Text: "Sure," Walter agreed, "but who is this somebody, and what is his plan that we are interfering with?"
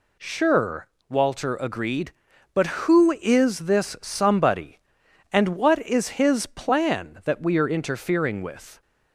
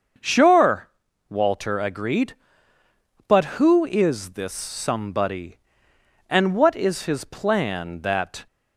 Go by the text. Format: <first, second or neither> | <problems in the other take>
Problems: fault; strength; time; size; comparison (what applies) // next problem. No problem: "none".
first | starts louder than the rest; until 1.6 s; 6.5 dB // stops before "we are interfering with"; at 8.4 s